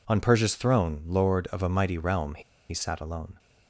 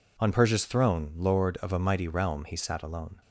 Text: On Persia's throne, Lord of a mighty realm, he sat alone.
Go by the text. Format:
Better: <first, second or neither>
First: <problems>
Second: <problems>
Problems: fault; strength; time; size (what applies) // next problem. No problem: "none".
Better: second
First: pauses between "he" and "sat"; slight; at 2.4 s; 0.29 s long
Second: none